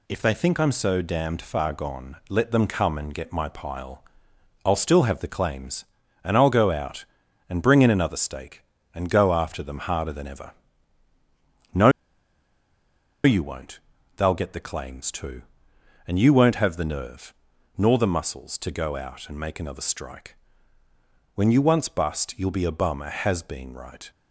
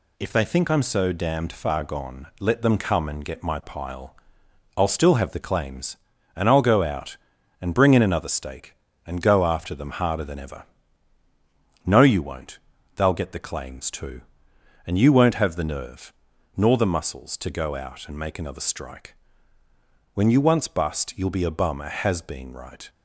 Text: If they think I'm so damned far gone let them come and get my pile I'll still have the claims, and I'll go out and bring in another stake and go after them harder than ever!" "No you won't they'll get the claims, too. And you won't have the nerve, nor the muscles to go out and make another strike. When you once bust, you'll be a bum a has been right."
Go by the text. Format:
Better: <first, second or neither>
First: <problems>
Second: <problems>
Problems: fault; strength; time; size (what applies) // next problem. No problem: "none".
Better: second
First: pauses between "pile" and "I'll"; noticeable; at 4.0 s; 0.60 s long // pauses between "No" and "you"; strong; at 11.8 s; 1.3 s long // pauses between "won't" and "they'll"; at 13.7 s; 0.38 s long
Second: pauses between "pile" and "I'll"; noticeable; at 4.1 s; 0.60 s long // pauses between "won't" and "they'll"; at 12.5 s; 0.38 s long